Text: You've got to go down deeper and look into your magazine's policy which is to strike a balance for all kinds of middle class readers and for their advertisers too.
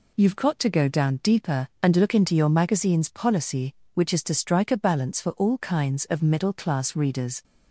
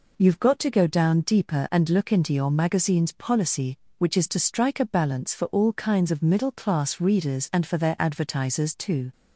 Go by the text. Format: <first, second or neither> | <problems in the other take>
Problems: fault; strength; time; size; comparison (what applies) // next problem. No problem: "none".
second | stops before "and for their advertisers too"; at 7.4 s